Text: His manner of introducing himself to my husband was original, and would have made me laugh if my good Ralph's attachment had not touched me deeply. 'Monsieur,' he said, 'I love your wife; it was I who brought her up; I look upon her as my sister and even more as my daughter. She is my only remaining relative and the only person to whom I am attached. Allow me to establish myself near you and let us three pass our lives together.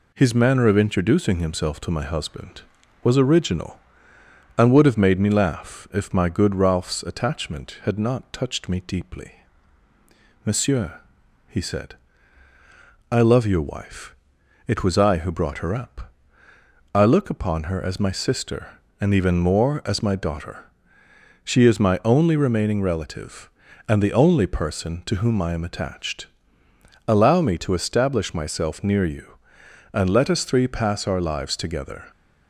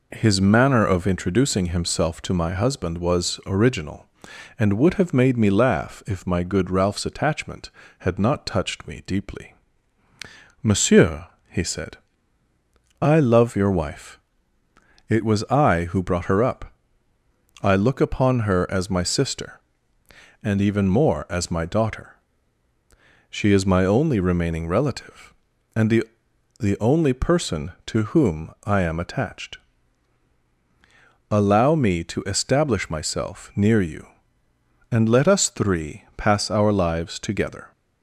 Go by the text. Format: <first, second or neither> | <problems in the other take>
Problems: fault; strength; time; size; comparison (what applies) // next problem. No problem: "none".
first | says "the" twice; at 26.5 s